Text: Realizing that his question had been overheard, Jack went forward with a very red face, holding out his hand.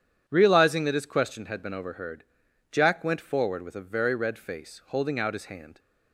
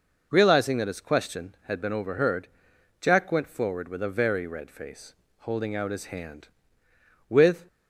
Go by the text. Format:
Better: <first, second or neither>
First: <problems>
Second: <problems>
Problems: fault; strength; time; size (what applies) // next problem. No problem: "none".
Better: first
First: none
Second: goes on to say "With"; slight; from 7.2 s on; 0.38 s long